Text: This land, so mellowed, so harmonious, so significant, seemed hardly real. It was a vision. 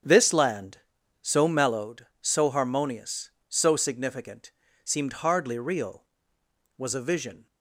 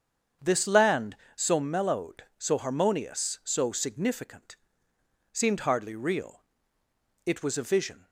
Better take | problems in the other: second | starts louder than the rest; strong; until 1.4 s; 8 dB; strong in the second // skips "It"; at 6.4 s

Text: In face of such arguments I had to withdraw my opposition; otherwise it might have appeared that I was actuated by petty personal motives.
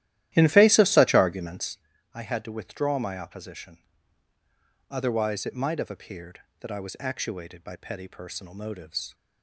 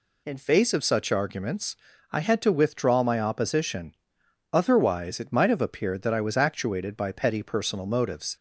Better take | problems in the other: second | starts louder than the rest; strong; until 2.0 s; 13.5 dB // pauses between "arguments" and "I"; at 1.7 s; 0.38 s long; slight in the second

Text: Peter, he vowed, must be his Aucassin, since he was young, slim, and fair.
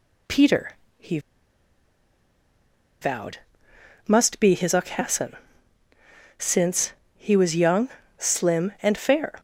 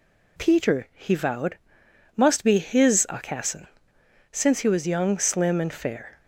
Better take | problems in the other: second | pauses between "he" and "vowed"; strong; at 1.1 s; 1.8 s long // pauses between "since" and "he"; slight; at 6.9 s; 0.24 s long

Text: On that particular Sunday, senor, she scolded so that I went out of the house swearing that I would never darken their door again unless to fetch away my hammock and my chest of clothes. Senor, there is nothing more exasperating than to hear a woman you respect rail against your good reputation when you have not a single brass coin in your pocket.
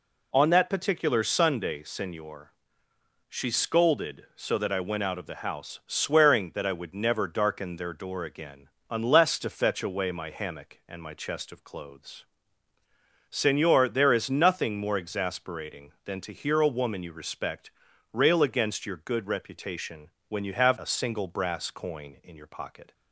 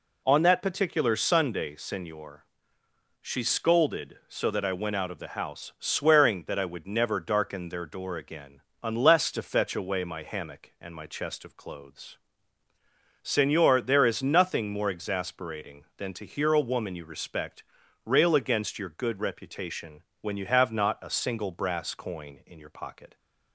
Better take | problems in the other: second | pauses between "again" and "unless"; slight; at 8.6 s; 0.20 s long; slight in the second // pauses between "respect" and "rail"; at 17.7 s; 0.42 s long; also in the second // pauses between "reputation" and "when"; slight; at 20.1 s; 0.18 s long; slight in the second // skips "not"; at 20.7 s

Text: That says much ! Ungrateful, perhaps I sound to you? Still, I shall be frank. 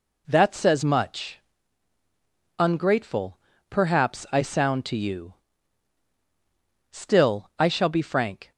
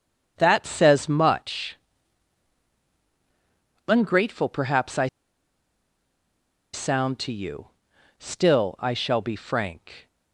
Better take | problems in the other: first | starts louder than the rest; strong; until 1.3 s; 7.5 dB // pauses between "I" and "sound"; strong; at 5.0 s; 1.6 s long

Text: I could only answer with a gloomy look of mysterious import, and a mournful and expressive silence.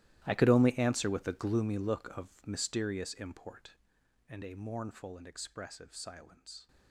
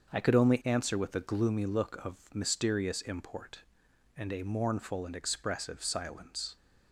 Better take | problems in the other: second | gets quieter; strong; throughout; 18.5 dB // starts louder than the rest; strong; until 1.2 s; 15 dB; also in the second

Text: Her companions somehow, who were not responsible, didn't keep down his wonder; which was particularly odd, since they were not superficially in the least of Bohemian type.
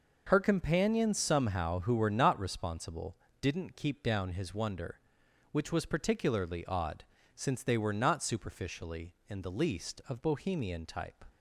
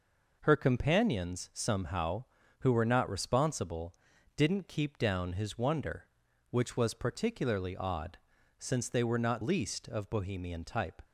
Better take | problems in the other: first | skips "superficially in the"; at 9.4 s

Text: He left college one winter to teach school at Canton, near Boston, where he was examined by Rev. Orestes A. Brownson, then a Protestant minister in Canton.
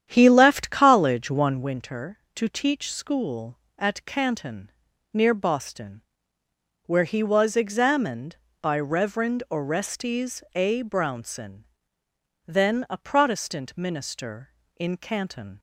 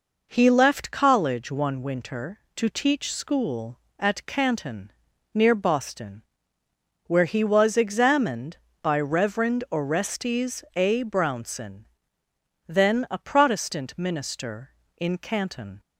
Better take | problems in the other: second | starts louder than the rest; strong; until 1.8 s; 9.5 dB

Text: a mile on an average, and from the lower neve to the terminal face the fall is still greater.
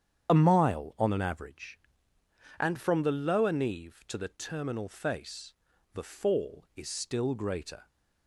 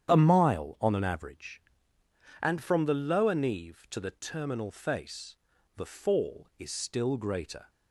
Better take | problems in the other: second | loses the start of "a"; at 0.2 s; 40 ms // starts louder than the rest; strong; until 1.3 s; 9 dB; strong in the second // pauses between "face" and "the"; at 5.5 s; 0.42 s long; also in the second

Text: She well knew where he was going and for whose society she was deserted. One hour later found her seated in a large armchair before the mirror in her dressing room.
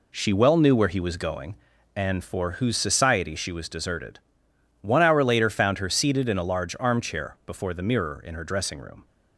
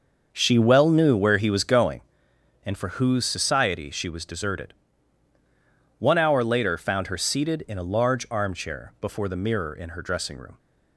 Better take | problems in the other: first | starts louder than the rest; noticeable; until 1.9 s; 6 dB

